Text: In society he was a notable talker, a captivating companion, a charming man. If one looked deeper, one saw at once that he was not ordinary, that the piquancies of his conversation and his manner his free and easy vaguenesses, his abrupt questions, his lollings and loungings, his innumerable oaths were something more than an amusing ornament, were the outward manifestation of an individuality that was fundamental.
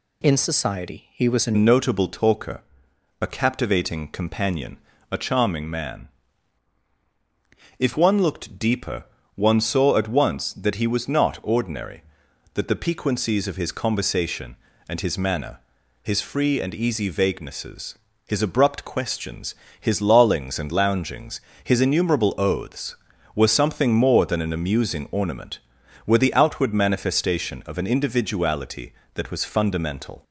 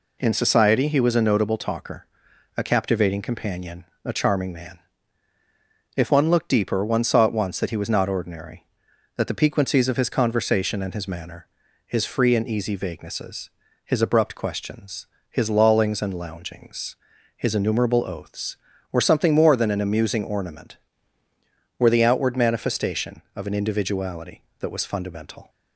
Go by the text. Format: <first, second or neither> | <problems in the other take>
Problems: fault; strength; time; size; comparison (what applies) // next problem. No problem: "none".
second | changes voice at "notable"; from 1.5 s on; 28.7 s long // pauses between "manner" and "his"; at 15.5 s; 0.42 s long; also in the second